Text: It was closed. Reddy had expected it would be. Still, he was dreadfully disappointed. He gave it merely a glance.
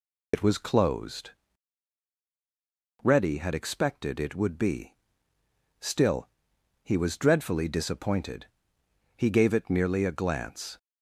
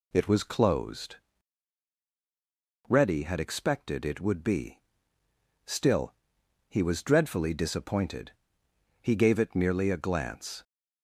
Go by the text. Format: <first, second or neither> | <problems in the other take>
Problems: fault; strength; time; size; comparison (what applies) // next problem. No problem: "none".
second | loses the start of "It"; at 0.3 s; 60 ms